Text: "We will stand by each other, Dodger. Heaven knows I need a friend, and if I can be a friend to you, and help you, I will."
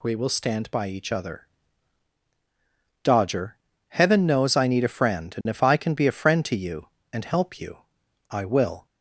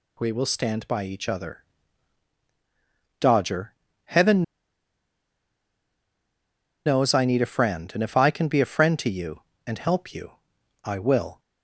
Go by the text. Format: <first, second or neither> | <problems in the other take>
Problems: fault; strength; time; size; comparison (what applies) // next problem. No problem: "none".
first | pauses between "Heaven" and "knows"; strong; at 4.4 s; 2.4 s long